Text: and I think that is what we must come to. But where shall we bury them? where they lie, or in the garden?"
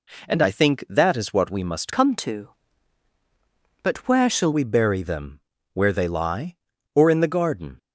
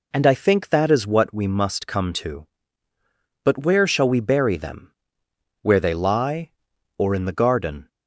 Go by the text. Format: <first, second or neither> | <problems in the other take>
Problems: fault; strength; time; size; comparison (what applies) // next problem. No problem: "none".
second | changes voice from "come" to "shall"; from 1.9 to 4.5 s; 2.6 s long